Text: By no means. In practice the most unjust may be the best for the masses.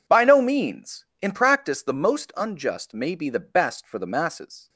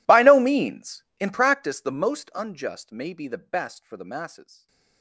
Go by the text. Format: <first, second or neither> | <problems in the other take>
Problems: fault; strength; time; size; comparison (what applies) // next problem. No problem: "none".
first | gets quieter; strong; throughout; 27 dB // stays silent after the last word; slight; from 4.4 s on; 0.6 s long